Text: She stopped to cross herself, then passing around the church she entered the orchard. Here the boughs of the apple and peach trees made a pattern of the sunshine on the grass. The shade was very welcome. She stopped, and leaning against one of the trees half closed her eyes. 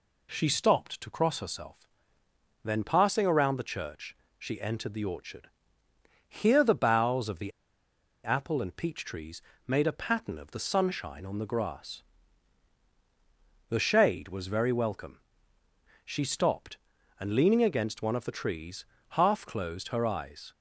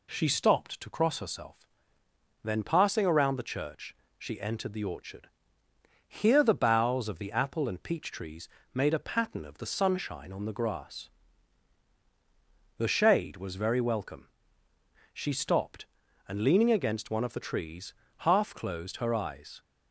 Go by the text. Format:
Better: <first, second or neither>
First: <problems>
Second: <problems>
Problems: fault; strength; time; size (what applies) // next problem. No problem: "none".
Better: second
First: pauses between "church" and "she"; slight; at 4.1 s; 0.24 s long // pauses between "the" and "apple"; noticeable; at 7.5 s; 0.73 s long // pauses between "trees" and "made"; slight; at 9.4 s; 0.26 s long // pauses between "trees" and "half"; slight; at 18.8 s; 0.24 s long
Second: pauses between "church" and "she"; slight; at 3.9 s; 0.24 s long // pauses between "trees" and "made"; slight; at 8.4 s; 0.26 s long // pauses between "trees" and "half"; slight; at 17.9 s; 0.24 s long